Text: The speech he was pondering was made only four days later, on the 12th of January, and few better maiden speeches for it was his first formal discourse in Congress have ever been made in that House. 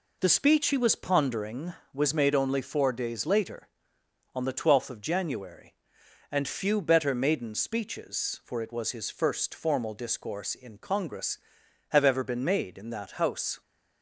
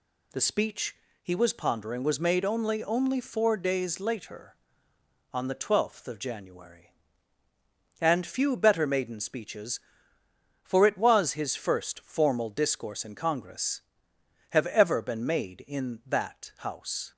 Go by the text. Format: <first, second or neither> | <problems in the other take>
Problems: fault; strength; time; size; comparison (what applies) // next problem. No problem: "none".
first | pauses between "speech" and "he"; slight; at 0.9 s; 0.26 s long // says "only" twice; at 2.8 s